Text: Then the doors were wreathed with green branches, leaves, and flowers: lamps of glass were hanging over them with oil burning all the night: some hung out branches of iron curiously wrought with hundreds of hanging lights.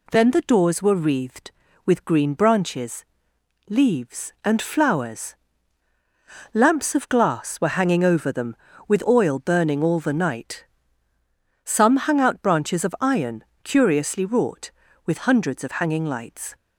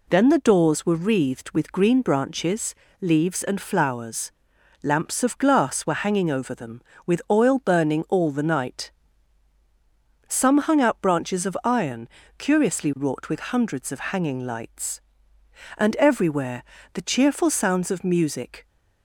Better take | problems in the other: first | pauses between "iron" and "curiously"; slight; at 12.0 s; 0.30 s long; slight in the first // goes on to say "And everywhere the cheerful sounds of music"; strong; from 15.7 s on; 2.9 s long

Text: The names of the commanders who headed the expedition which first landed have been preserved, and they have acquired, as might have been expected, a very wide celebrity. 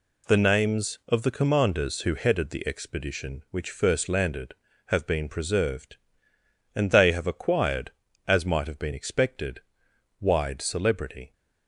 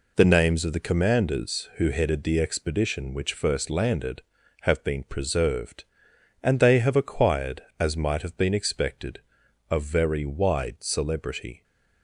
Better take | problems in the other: second | skips "a very"; at 9.9 s

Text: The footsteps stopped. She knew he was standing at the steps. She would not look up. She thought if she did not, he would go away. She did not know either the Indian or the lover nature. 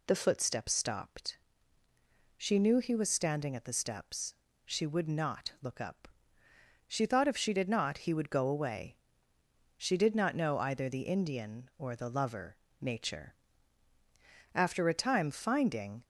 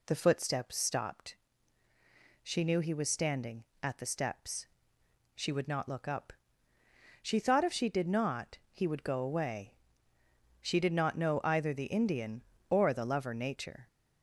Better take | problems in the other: second | pauses between "lover" and "nature"; slight; at 12.5 s; 0.24 s long // goes on to say "After a time finding"; from 14.5 s on; 1.5 s long

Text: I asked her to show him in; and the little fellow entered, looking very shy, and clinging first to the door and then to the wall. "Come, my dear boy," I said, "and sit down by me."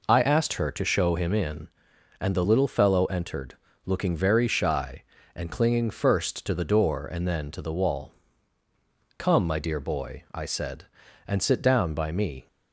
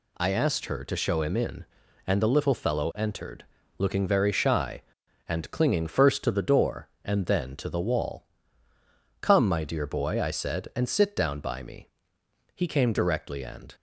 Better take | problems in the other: first | goes on to say "He came directly and"; noticeable; from 12.5 s on; 1.2 s long

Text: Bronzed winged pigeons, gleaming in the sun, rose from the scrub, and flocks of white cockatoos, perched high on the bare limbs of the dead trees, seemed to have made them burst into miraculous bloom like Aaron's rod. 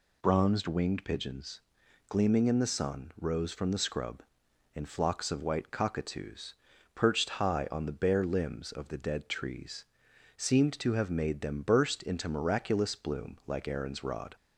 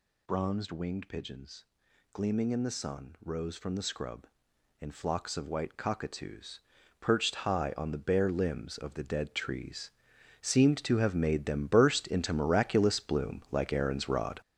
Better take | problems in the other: first | gets louder; strong; throughout; 8 dB

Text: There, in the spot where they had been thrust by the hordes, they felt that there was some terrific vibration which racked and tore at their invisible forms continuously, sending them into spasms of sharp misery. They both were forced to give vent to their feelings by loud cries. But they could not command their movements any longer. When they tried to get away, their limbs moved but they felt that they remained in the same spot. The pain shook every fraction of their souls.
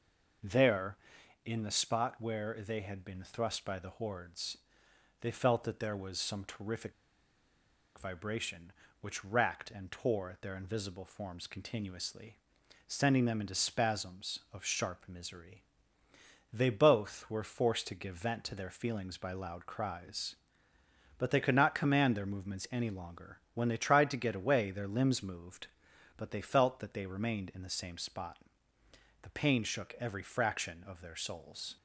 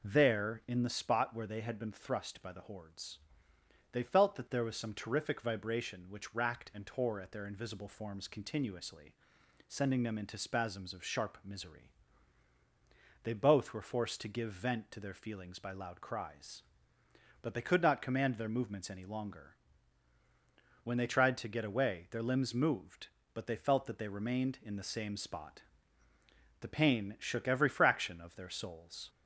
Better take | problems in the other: second | pauses between "terrific" and "vibration"; at 6.9 s; 1.0 s long

